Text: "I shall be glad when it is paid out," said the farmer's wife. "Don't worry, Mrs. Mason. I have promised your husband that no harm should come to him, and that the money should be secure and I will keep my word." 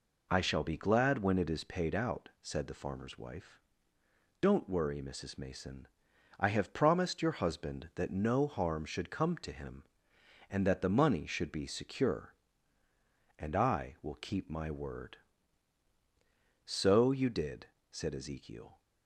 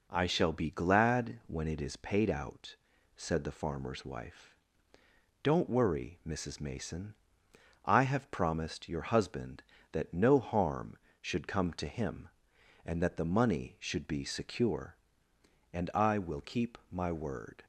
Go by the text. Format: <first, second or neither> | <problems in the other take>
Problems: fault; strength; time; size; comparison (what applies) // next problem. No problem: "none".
second | goes on to say "So you did said Ezekiel"; strong; from 16.6 s on; 2.1 s long